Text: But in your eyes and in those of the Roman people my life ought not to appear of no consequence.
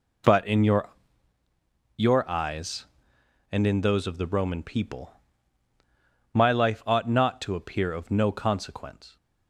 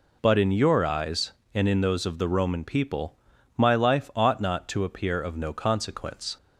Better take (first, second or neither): second